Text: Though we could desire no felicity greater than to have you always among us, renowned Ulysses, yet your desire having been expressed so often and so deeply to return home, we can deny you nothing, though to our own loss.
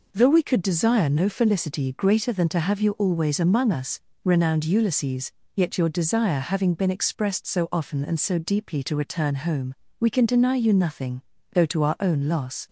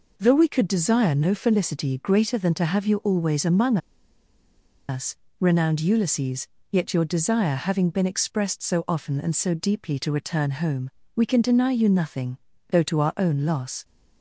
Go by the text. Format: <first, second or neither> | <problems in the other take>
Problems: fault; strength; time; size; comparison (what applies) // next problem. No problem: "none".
first | pauses between "among" and "us"; at 3.7 s; 1.1 s long